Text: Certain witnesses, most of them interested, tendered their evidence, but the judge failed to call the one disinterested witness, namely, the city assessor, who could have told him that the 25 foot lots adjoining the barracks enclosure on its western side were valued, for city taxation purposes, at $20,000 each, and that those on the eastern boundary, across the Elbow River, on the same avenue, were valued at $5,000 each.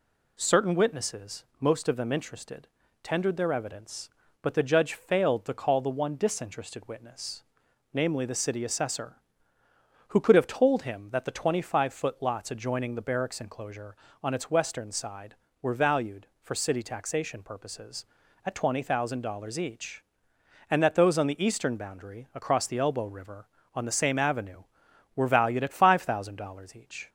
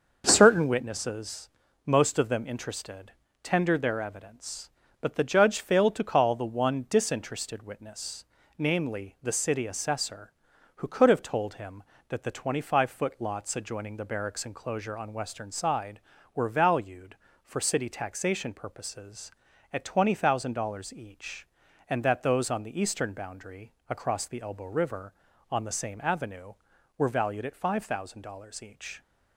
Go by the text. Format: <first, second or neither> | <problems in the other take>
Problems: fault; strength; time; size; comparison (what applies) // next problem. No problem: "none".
first | starts louder than the rest; until 1.2 s; 6.5 dB // skips "its"; at 15.1 s